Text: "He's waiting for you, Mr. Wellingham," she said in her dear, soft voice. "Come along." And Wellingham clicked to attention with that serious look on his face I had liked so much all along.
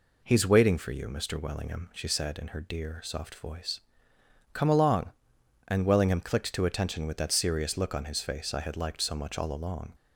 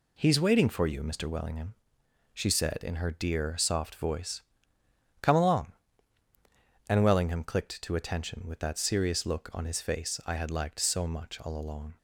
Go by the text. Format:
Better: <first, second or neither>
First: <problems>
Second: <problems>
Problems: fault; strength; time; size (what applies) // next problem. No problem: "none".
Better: neither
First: none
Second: none